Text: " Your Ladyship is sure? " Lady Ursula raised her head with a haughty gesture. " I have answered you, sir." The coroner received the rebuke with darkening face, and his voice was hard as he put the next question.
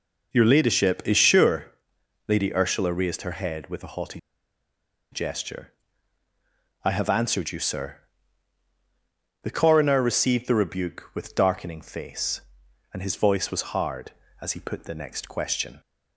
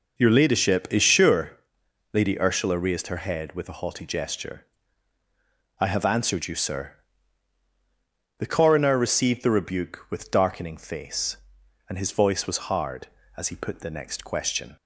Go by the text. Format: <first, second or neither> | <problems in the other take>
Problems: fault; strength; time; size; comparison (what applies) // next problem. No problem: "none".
second | pauses between "haughty" and "gesture"; noticeable; at 4.1 s; 0.93 s long